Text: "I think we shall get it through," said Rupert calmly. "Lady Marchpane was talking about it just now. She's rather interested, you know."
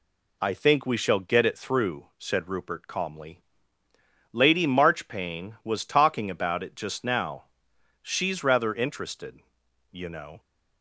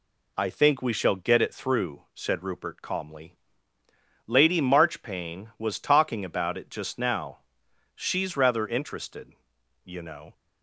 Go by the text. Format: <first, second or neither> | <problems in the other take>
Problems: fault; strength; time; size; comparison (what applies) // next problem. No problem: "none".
neither | none